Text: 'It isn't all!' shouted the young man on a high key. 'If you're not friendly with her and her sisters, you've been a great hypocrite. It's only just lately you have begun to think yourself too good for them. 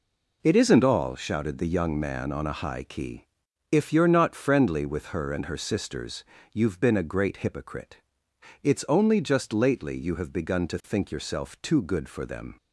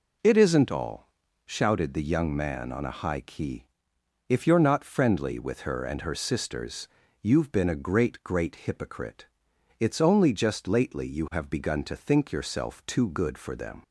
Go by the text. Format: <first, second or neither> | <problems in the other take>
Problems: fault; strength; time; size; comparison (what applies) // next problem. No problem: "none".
first | says "great" twice; at 8.2 s